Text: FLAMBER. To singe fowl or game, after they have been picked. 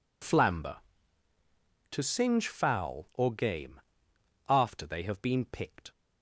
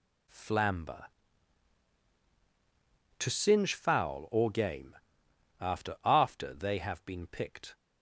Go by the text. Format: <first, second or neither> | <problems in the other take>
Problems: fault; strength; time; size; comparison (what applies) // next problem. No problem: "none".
first | says "after" twice; at 6.0 s